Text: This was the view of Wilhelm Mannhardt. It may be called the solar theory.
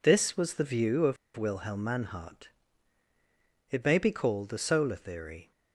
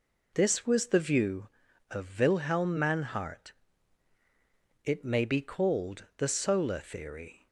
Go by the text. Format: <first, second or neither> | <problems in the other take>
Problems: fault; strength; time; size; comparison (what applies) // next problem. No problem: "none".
second | pauses between "of" and "Wilhelm"; slight; at 1.1 s; 0.20 s long